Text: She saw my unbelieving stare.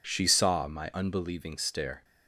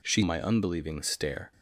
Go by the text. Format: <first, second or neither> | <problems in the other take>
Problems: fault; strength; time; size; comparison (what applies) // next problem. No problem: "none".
first | skips "saw"; at 0.2 s